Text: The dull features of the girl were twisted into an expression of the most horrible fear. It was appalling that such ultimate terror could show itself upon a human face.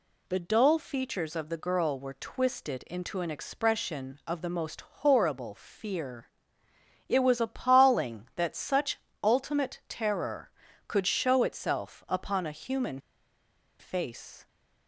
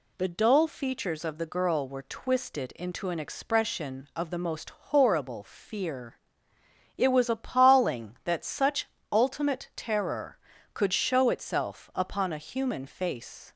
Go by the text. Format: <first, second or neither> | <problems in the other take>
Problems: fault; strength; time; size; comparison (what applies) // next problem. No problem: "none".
second | pauses between "such" and "ultimate"; slight; at 8.9 s; 0.24 s long; slight in the second // pauses between "human" and "face"; noticeable; at 12.9 s; 0.81 s long